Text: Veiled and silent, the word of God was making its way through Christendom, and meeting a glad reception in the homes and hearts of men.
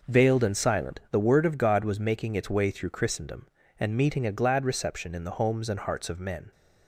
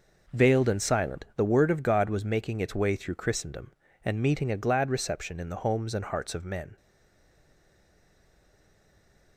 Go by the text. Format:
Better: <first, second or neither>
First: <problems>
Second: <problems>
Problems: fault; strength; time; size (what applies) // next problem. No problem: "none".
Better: first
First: none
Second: stays silent after the last word; strong; from 6.7 s on; 2.6 s long